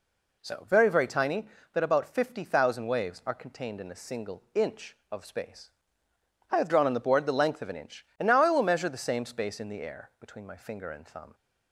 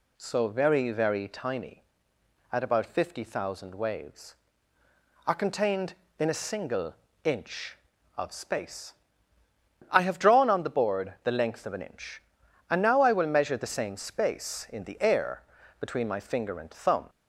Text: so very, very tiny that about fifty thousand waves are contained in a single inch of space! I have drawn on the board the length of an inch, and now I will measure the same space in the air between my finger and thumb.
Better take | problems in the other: first | says "at" for "that"; at 2.5 s // pauses between "single" and "inch"; slight; at 6.9 s; 0.30 s long // pauses between "air" and "between"; at 15.4 s; 0.38 s long

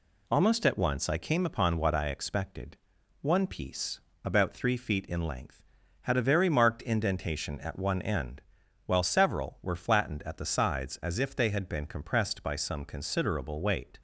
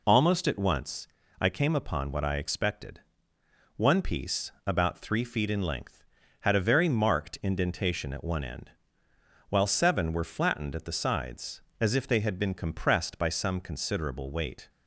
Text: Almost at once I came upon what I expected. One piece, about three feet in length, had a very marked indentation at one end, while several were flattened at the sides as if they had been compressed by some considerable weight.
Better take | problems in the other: first | pauses between "once" and "I"; slight; at 1.0 s; 0.32 s long // says "seven" for "several"; at 9.6 s

